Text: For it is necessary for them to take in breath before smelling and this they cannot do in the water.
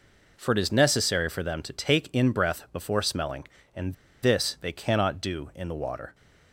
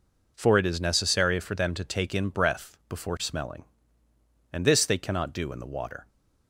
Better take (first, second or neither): second